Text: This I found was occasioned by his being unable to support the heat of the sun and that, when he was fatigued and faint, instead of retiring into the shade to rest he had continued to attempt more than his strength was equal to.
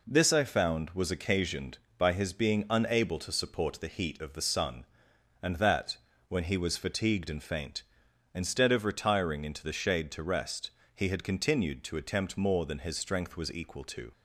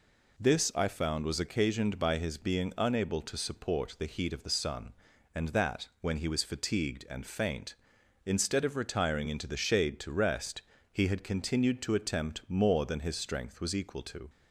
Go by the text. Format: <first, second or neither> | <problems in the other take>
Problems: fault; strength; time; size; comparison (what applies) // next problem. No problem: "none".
neither | pauses between "rest" and "he"; slight; the same in both